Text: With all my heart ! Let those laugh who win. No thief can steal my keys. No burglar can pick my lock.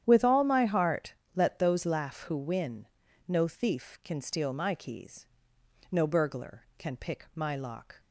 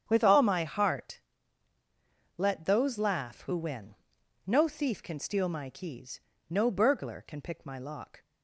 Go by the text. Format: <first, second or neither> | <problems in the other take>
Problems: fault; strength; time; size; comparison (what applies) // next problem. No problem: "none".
neither | starts louder than the rest; strong; the same in both